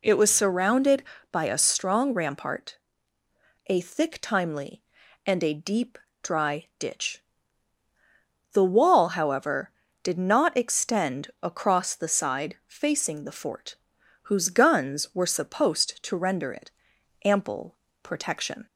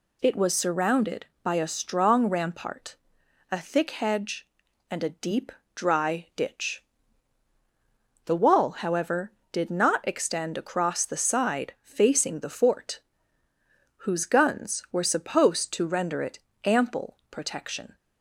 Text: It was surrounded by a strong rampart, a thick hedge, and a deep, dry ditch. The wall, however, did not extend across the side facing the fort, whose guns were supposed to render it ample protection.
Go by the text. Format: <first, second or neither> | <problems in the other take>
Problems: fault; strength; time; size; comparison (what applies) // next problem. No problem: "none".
second | says "timely" for "hedge"; at 4.1 s // pauses between "it" and "ample"; noticeable; at 16.6 s; 0.54 s long; slight in the second // pauses between "ample" and "protection"; slight; at 17.7 s; 0.24 s long